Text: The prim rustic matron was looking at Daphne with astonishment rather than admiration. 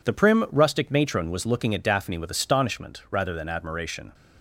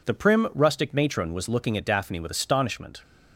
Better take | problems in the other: first | stops before "rather than admiration"; at 3.0 s

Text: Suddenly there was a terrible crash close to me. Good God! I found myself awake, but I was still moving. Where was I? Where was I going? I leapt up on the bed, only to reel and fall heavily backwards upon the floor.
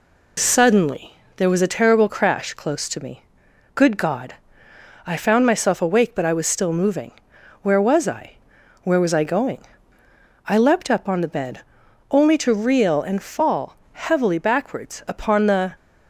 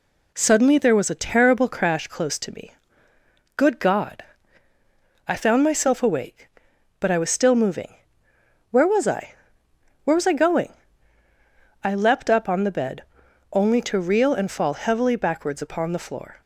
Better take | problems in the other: second | pauses between "Suddenly" and "there"; slight; at 1.1 s; 0.24 s long // pauses between "fall" and "heavily"; slight; at 13.7 s; 0.22 s long // stops before "floor"; at 15.7 s

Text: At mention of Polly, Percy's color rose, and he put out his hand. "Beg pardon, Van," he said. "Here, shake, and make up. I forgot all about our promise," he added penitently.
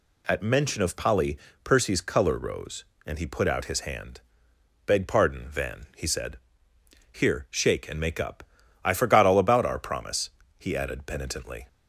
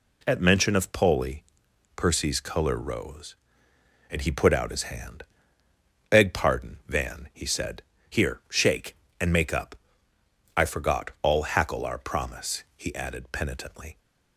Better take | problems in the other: first | says "hackle" for "about"; at 11.4 s

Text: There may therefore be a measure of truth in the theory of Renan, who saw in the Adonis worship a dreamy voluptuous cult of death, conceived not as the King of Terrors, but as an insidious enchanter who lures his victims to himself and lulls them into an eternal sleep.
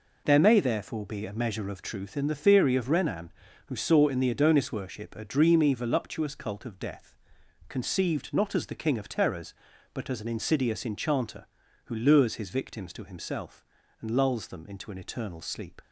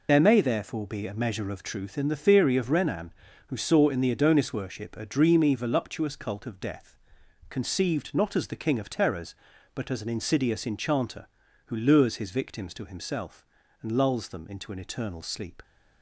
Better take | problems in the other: first | loses the start of "There"; at 0.0 s; 30 ms

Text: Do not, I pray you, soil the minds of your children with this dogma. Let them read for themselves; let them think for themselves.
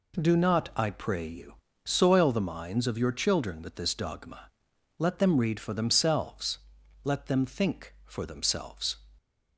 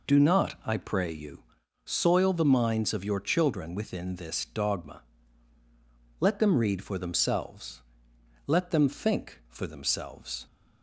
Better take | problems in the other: first | says "within" for "with"; at 3.7 s

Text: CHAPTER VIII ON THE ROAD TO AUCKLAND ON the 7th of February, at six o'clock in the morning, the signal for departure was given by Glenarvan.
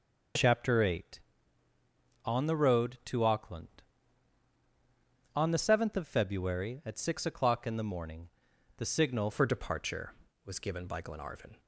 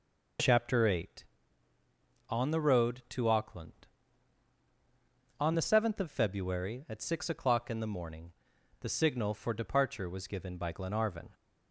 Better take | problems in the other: second | changes voice at "for"; from 9.3 s on; 2.2 s long

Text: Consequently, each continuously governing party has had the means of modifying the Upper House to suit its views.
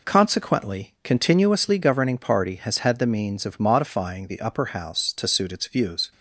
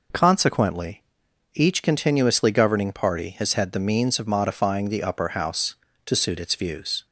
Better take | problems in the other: second | skips "each"; at 0.9 s

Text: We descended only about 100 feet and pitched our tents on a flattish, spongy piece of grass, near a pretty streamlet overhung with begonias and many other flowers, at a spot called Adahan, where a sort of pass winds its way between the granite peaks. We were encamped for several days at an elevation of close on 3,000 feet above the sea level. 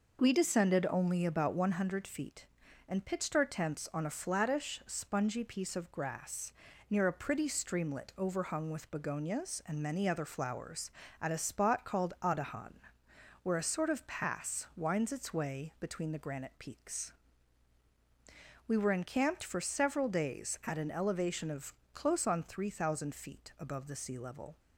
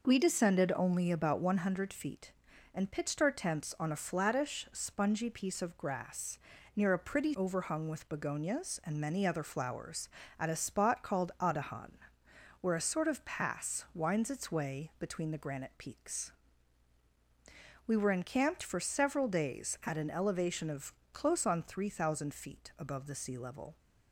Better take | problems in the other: first | skips "streamlet"; at 7.3 s // pauses between "of" and "close"; slight; at 20.9 s; 0.20 s long; slight in the first

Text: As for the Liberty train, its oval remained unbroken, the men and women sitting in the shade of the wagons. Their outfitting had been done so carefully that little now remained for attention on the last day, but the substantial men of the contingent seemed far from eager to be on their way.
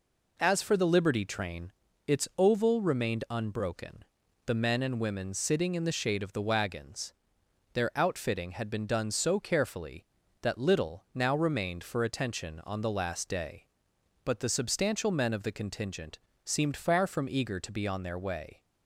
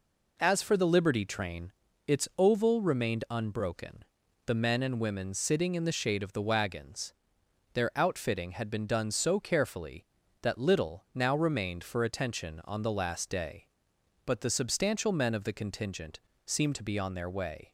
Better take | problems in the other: first | pauses between "contingent" and "seemed"; slight; at 16.1 s; 0.26 s long; slight in the first // skips "far from eager"; at 16.7 s

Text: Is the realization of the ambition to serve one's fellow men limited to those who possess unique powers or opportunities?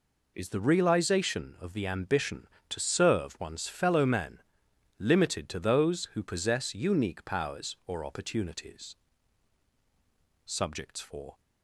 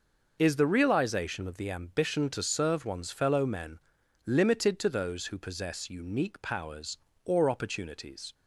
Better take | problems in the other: second | pauses between "men" and "limited"; noticeable; at 4.4 s; 0.58 s long; noticeable in the second // goes on to say "Subjects for"; noticeable; from 10.4 s on; 0.94 s long

